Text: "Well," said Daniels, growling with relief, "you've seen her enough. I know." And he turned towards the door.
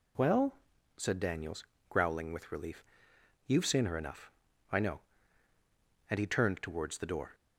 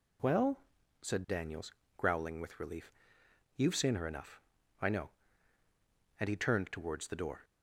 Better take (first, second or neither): neither